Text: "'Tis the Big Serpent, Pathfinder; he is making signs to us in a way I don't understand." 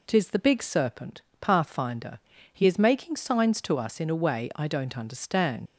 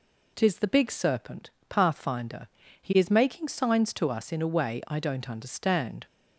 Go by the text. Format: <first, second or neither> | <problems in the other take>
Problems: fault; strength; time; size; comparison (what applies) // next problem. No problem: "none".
second | leaves "understand" unfinished; at 5.6 s; 75 ms